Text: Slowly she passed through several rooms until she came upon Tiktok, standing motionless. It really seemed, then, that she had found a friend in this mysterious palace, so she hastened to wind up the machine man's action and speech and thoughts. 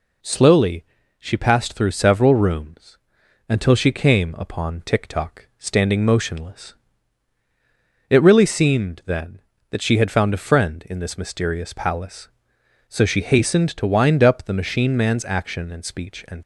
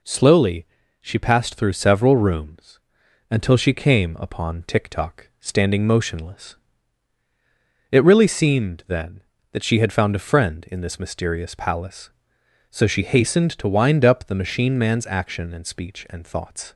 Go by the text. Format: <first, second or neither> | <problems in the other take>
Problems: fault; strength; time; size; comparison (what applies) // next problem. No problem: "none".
second | pauses between "Slowly" and "she"; slight; at 0.8 s; 0.34 s long; slight in the second // pauses between "rooms" and "until"; noticeable; at 2.9 s; 0.52 s long; noticeable in the second // stops before "thoughts"; at 16.4 s